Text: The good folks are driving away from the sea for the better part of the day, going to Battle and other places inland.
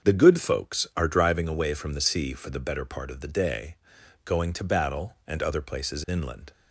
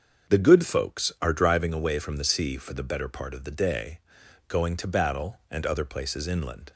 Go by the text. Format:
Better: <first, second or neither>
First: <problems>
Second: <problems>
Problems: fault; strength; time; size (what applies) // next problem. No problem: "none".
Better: neither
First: starts louder than the rest; until 1.1 s; 7 dB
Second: starts louder than the rest; until 1.3 s; 7 dB